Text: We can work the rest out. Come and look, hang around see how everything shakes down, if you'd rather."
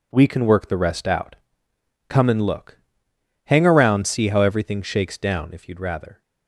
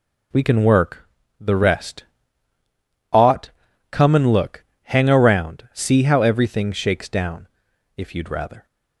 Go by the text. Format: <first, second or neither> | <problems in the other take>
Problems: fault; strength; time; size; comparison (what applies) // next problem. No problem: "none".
first | pauses between "work" and "the"; slight; at 1.0 s; 0.32 s long // says "ought" for "out"; at 3.1 s